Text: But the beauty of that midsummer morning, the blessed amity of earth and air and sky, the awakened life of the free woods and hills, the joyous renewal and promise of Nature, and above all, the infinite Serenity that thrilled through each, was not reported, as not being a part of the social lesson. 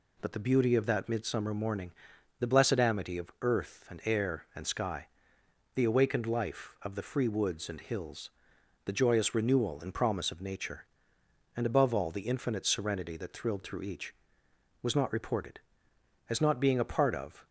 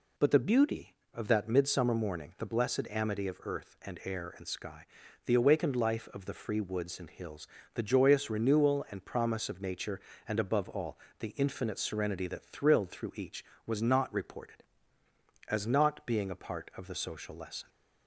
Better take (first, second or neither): second